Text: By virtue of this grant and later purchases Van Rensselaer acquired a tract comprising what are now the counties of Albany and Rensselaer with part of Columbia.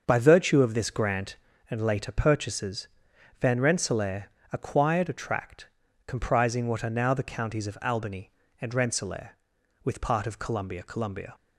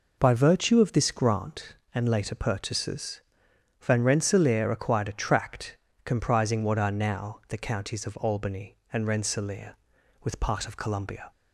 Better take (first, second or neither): second